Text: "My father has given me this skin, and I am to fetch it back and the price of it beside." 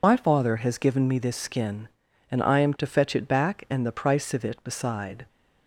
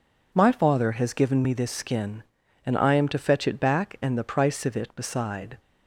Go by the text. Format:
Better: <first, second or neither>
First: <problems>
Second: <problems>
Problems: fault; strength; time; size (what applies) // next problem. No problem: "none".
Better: second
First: loses the start of "My"; at 0.0 s; 50 ms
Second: none